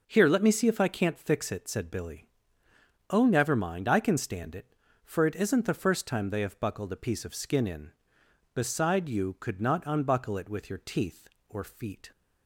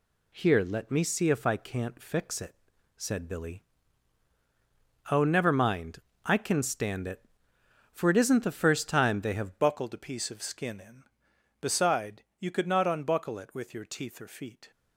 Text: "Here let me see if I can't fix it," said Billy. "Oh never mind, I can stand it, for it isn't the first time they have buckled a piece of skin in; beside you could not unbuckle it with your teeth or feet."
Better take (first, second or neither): first